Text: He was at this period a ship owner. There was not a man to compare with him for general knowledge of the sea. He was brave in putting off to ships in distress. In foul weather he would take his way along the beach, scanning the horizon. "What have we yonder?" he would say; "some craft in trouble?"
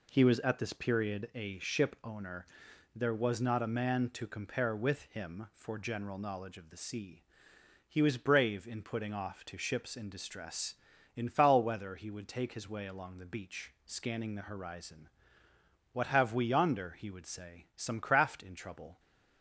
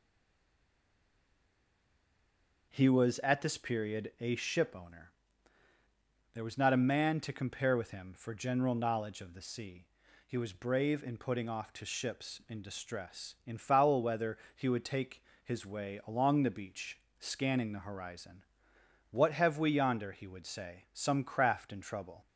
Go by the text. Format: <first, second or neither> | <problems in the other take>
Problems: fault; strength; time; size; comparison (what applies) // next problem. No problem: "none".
first | stays silent before the first word; strong; until 2.6 s; 2.6 s long // pauses between "weather" and "he"; slight; at 14.3 s; 0.18 s long // pauses between "take" and "his"; slight; at 15.2 s; 0.20 s long